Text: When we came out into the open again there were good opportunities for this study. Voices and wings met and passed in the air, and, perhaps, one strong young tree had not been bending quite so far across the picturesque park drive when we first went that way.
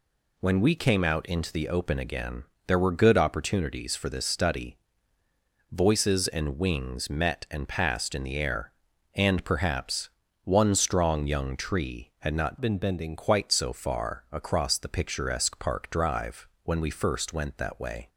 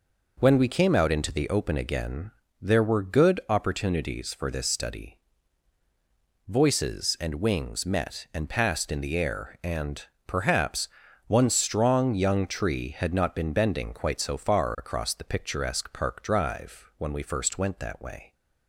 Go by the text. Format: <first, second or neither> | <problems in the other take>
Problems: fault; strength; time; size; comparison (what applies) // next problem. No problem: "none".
second | pauses between "again" and "there"; slight; at 2.4 s; 0.22 s long; slight in the second // changes voice from "been" to "bending"; from 12.6 to 13.1 s; 0.5 s long // pauses between "drive" and "when"; slight; at 16.4 s; 0.16 s long